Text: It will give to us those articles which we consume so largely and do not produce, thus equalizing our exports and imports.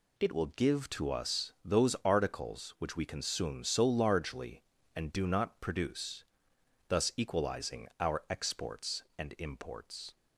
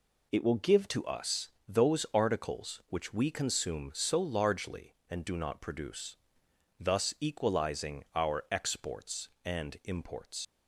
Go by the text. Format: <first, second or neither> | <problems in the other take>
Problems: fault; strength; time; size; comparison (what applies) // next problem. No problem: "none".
first | pauses between "us" and "those"; slight; at 1.4 s; 0.20 s long // leaves "imports" unfinished; at 10.4 s; 120 ms